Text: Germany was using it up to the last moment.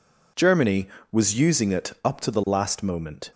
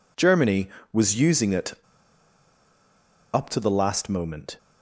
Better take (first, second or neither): first